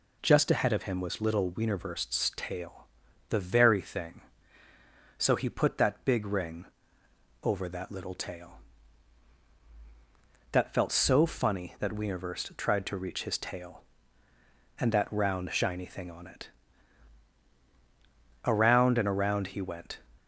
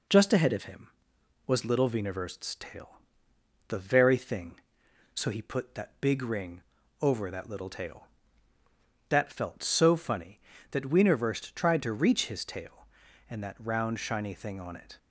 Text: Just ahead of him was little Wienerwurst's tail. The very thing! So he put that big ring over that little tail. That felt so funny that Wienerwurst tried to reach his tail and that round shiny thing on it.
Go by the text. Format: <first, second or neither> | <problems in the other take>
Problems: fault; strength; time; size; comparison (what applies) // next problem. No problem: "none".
second | pauses between "ring" and "over"; noticeable; at 6.6 s; 0.78 s long; also in the second // goes on to say "Around and around he went"; from 18.4 s on; 1.5 s long